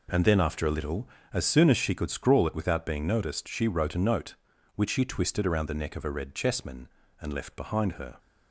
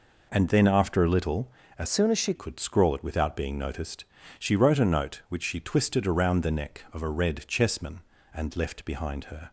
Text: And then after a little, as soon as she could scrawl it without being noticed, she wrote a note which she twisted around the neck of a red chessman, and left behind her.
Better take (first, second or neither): first